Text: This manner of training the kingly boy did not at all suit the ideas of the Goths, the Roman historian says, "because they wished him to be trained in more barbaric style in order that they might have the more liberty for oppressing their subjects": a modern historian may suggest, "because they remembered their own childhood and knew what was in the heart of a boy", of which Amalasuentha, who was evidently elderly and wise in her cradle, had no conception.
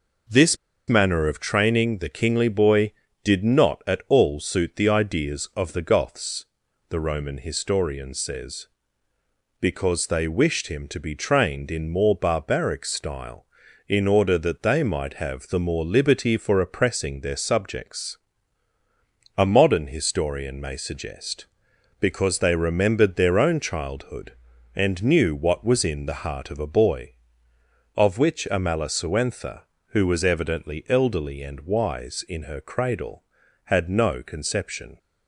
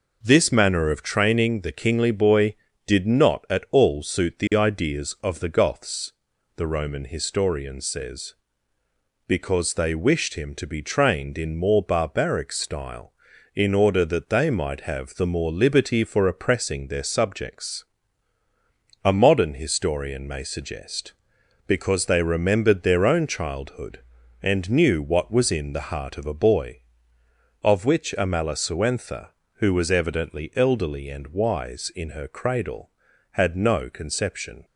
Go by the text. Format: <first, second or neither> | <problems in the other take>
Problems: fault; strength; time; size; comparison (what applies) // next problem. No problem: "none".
second | pauses between "This" and "manner"; slight; at 0.5 s; 0.33 s long